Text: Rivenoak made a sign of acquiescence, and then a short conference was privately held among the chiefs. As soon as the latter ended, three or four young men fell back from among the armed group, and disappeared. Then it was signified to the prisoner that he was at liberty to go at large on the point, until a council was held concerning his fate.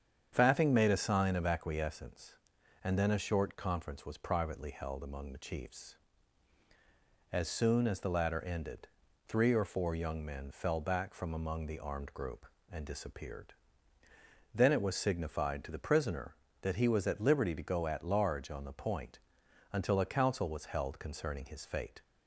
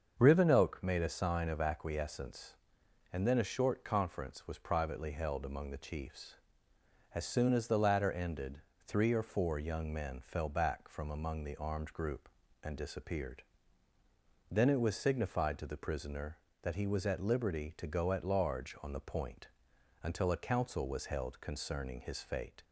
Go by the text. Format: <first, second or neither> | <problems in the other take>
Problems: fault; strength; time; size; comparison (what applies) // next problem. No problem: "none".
second | starts louder than the rest; strong; until 1.3 s; 8 dB; also in the second // says "Faffing" for "Rivenoak"; at 0.3 s